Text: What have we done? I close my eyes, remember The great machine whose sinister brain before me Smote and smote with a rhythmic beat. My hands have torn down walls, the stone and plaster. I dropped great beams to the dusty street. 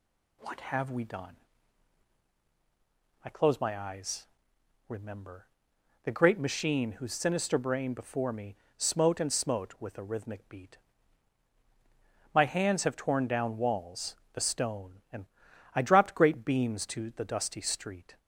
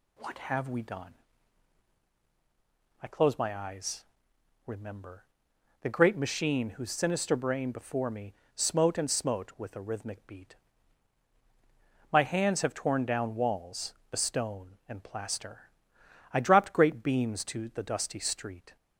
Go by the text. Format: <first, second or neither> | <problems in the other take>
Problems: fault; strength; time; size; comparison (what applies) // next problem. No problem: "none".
second | pauses between "remember" and "The"; noticeable; at 5.4 s; 0.56 s long; noticeable in the second // pauses between "me" and "Smote"; slight; at 8.5 s; 0.22 s long; slight in the second // skips "plaster"; at 15.5 s